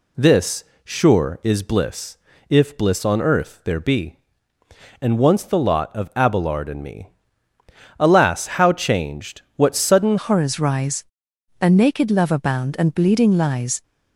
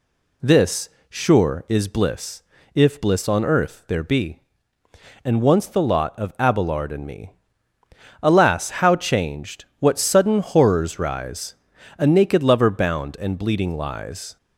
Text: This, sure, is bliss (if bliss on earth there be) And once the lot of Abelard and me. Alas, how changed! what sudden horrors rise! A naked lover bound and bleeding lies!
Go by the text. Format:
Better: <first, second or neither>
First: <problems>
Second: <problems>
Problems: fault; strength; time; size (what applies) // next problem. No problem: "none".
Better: second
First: changes voice at "horrors"; from 10.1 s on; 3.7 s long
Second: none